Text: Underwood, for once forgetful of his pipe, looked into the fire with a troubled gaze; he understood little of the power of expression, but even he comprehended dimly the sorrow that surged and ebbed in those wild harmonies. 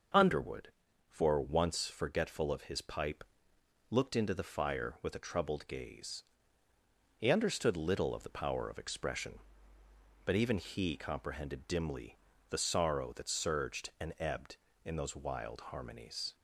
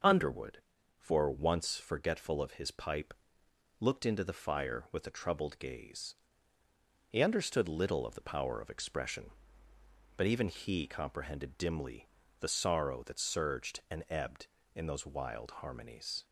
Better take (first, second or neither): neither